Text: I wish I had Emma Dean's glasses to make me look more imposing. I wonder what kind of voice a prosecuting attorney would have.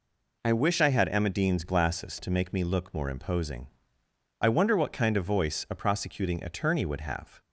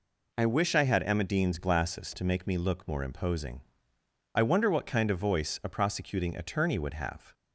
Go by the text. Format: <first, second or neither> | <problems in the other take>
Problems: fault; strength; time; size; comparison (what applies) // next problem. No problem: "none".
neither | none